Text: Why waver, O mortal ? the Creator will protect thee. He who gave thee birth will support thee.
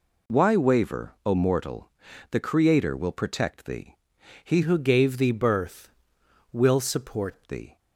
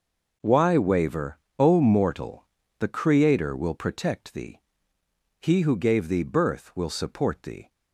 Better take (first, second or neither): second